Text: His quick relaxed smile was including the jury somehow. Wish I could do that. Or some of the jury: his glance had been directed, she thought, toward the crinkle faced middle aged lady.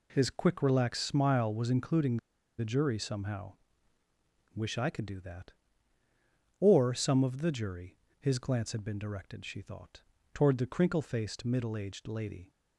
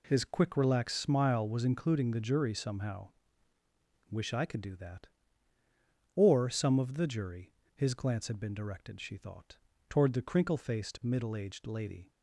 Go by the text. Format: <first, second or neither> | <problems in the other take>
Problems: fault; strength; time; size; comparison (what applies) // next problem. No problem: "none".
second | pauses between "including" and "the"; at 2.1 s; 0.41 s long